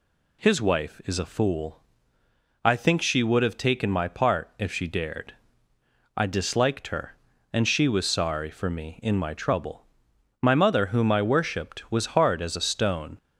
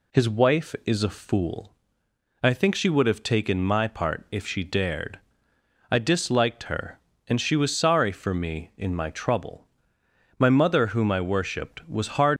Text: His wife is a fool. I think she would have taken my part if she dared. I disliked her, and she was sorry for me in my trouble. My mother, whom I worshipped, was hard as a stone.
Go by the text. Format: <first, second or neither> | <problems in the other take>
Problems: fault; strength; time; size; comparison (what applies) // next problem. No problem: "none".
first | stops before "as a stone"; at 12.3 s